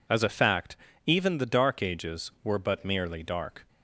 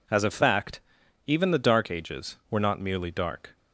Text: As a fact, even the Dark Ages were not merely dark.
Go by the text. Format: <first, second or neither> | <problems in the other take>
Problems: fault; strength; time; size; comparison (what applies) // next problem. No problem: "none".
second | says "but" for "not"; at 2.5 s